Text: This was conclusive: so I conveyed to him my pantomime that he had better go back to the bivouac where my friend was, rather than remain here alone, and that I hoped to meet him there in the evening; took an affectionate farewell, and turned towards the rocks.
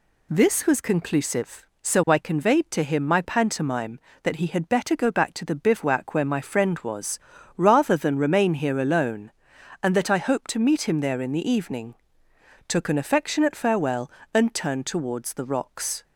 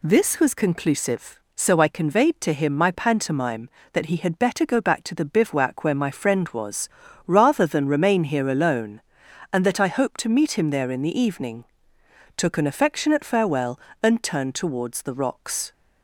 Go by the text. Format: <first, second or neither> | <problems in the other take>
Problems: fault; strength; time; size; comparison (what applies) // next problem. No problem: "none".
neither | none